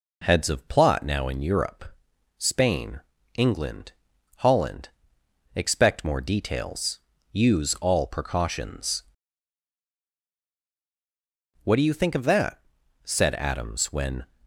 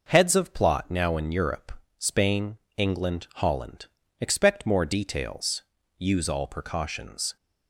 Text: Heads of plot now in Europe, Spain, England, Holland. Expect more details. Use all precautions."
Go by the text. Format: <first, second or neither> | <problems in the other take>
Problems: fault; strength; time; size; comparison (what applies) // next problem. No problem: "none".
second | goes on to say "What do you think of that said Adams when"; strong; from 11.6 s on; 2.6 s long